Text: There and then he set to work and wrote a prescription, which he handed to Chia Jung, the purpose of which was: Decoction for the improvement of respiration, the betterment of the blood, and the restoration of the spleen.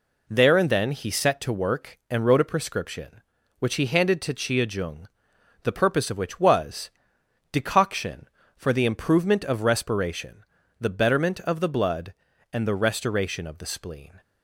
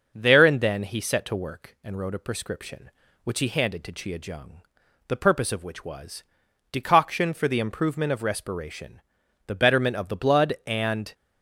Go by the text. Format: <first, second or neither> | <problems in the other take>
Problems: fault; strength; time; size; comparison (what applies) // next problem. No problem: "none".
first | starts louder than the rest; noticeable; until 1.1 s; 6 dB // stops before "the restoration of the spleen"; at 11.1 s